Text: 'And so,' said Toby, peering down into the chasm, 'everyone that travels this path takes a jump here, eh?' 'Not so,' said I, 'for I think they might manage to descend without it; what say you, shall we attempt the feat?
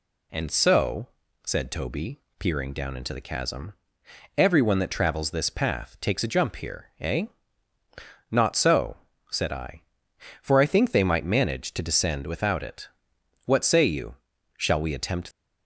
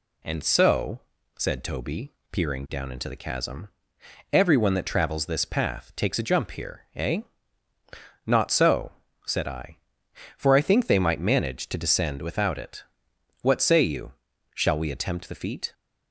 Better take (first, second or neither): second